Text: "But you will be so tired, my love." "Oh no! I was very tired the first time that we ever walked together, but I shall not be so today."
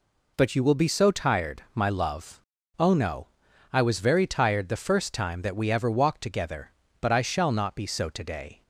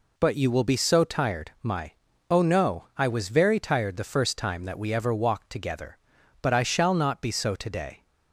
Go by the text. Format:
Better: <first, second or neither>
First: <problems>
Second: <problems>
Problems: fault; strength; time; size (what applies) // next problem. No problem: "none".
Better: first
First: none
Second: skips "love"; at 2.1 s